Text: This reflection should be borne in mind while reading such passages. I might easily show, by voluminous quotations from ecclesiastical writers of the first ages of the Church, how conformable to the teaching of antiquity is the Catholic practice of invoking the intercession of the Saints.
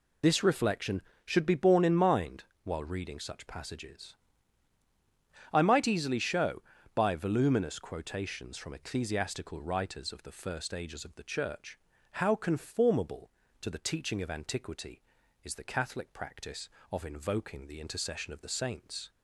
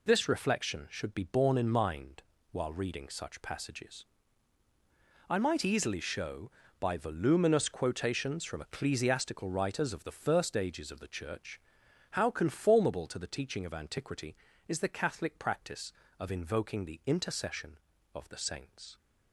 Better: second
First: loses the start of "This"; at 0.2 s; 50 ms // pauses between "mind" and "while"; slight; at 2.4 s; 0.20 s long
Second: pauses between "mind" and "while"; slight; at 2.2 s; 0.30 s long

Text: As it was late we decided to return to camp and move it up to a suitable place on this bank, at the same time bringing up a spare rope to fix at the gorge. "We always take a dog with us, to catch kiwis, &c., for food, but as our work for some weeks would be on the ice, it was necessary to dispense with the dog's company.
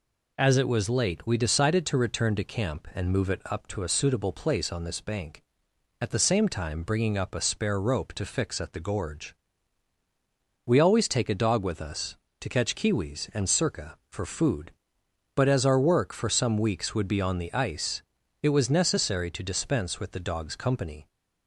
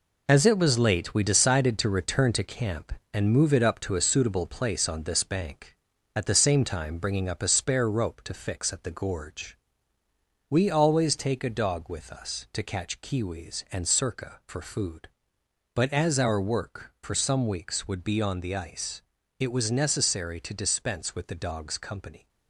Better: first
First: none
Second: gets quieter; strong; throughout; 8 dB

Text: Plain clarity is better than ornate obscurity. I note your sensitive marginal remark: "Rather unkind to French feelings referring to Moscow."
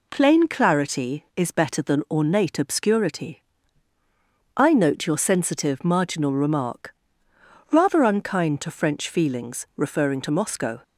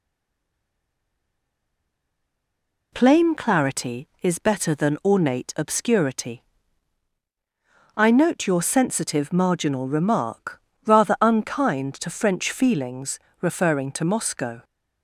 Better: first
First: none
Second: stays silent before the first word; strong; until 2.9 s; 2.9 s long // pauses between "feelings" and "referring"; slight; at 13.1 s; 0.24 s long

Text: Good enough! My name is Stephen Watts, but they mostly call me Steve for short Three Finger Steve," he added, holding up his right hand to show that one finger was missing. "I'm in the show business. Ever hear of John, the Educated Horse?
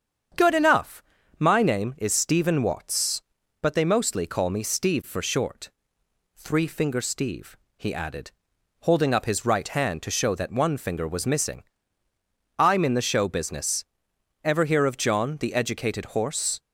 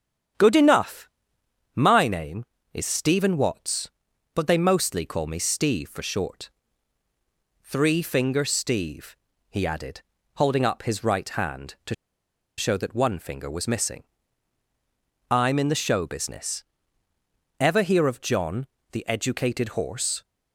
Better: first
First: starts louder than the rest; strong; until 1.7 s; 8 dB // pauses between "short" and "Three"; noticeable; at 5.6 s; 0.66 s long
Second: starts louder than the rest; strong; until 2.0 s; 9 dB // pauses between "short" and "Three"; at 6.4 s; 1.1 s long // pauses between "to" and "show"; noticeable; at 11.9 s; 0.63 s long

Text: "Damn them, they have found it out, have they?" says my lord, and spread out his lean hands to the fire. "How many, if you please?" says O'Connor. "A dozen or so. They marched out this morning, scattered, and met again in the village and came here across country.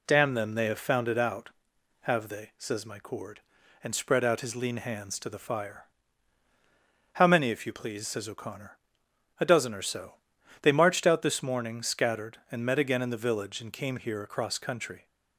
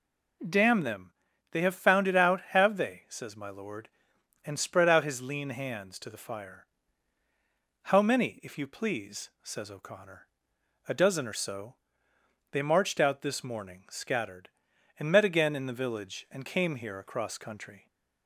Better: second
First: says "cord" for "lord"; at 2.9 s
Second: none

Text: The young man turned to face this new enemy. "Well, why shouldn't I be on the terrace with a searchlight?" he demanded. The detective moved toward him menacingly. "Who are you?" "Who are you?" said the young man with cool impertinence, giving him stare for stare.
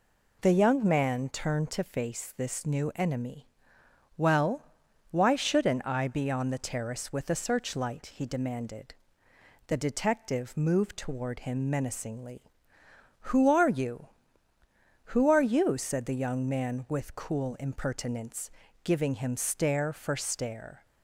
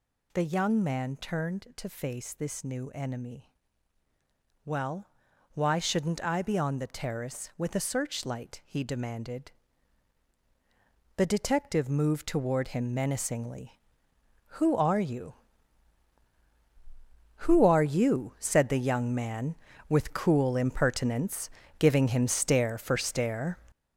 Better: first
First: none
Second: gets louder; strong; throughout; 8.5 dB

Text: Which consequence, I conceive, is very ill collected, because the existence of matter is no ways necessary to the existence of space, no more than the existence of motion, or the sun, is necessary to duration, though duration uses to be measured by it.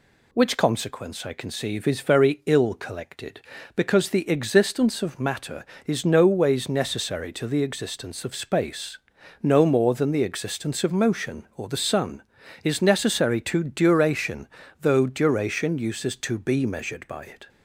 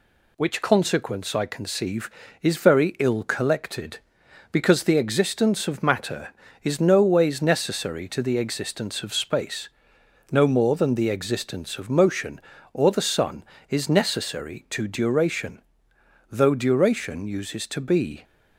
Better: first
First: none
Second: stops before "measured by it"; at 18.2 s

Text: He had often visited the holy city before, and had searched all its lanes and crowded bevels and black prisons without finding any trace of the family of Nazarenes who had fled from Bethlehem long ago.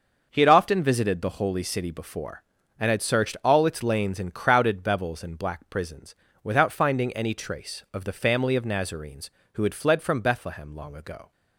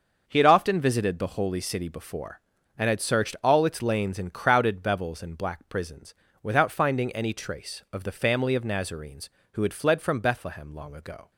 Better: neither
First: starts louder than the rest; until 1.3 s; 6 dB // pauses between "prisons" and "without"; slight; at 6.1 s; 0.28 s long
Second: starts louder than the rest; until 1.2 s; 6 dB // pauses between "prisons" and "without"; slight; at 6.1 s; 0.28 s long

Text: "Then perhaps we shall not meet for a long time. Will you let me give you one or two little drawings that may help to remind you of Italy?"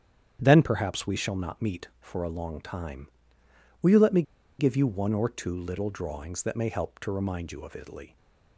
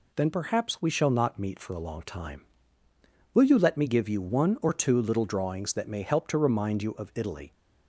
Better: second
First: starts louder than the rest; strong; until 1.4 s; 9 dB // pauses between "me" and "give"; at 4.2 s; 0.36 s long // stays silent after the last word; slight; from 8.0 s on; 0.5 s long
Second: none

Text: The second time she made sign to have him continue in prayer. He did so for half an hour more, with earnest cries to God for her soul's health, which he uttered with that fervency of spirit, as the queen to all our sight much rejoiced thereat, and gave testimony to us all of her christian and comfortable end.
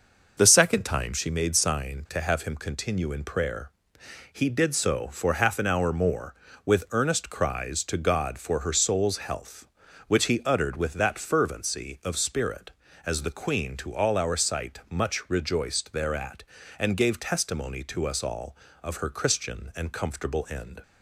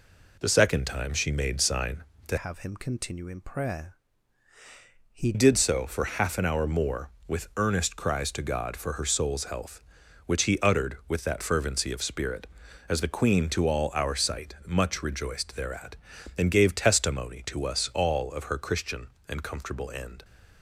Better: first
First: none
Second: changes voice from "have" to "He"; from 2.3 to 5.3 s; 3.0 s long

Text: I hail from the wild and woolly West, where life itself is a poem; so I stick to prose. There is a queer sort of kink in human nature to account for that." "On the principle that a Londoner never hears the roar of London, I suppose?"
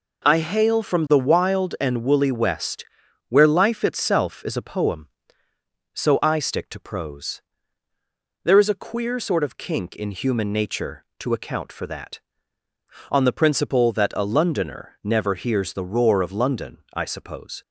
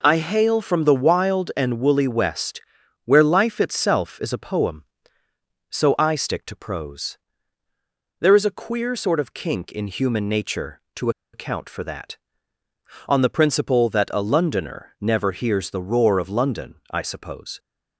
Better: first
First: none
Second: pauses between "to" and "account"; slight; at 11.0 s; 0.23 s long

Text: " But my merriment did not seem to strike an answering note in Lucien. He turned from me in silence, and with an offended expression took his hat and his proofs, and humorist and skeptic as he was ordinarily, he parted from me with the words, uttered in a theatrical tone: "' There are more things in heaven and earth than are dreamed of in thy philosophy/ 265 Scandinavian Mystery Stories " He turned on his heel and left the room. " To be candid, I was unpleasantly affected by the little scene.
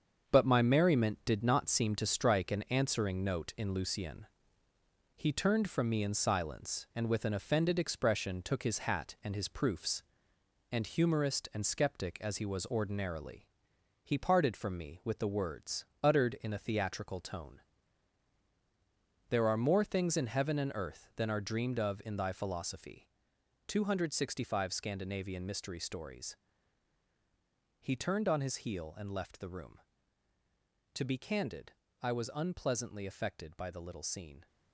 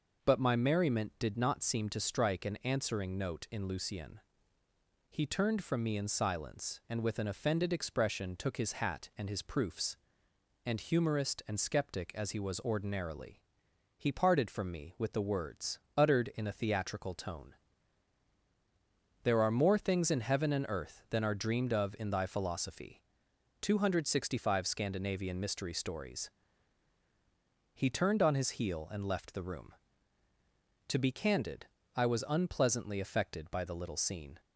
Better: second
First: gets quieter; strong; throughout; 13.5 dB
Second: none

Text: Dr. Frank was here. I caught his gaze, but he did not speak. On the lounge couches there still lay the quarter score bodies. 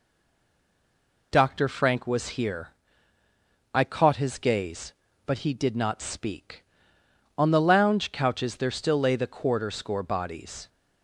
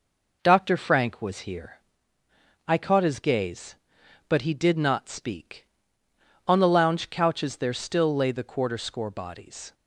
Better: second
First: stays silent before the first word; noticeable; until 1.3 s; 1.3 s long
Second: none

